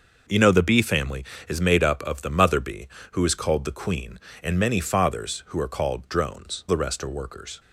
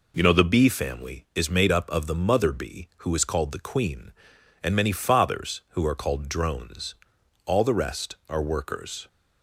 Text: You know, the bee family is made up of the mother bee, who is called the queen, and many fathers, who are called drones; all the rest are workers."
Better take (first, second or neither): second